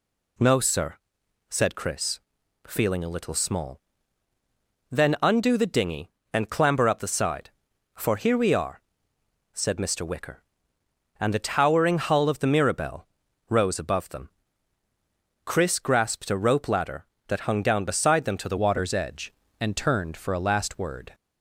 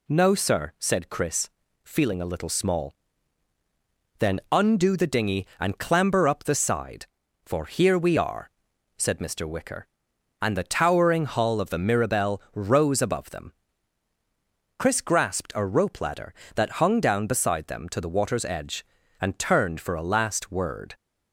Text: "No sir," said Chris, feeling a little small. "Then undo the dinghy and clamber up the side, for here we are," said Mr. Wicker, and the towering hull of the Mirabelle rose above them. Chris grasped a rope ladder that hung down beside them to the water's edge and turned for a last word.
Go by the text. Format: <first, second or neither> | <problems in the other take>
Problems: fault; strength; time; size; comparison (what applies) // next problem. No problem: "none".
second | pauses between "Mirabelle" and "rose"; at 13.0 s; 0.42 s long // changes voice at "water's"; from 18.5 s on; 2.6 s long